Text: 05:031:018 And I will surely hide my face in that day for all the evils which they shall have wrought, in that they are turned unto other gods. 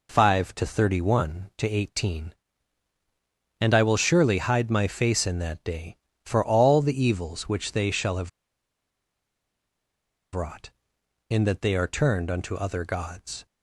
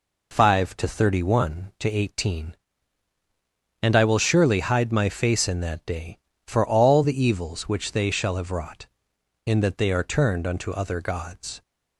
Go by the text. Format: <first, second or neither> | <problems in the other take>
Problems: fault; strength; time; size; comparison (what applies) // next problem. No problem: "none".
second | pauses between "have" and "wrought"; strong; at 8.2 s; 2.0 s long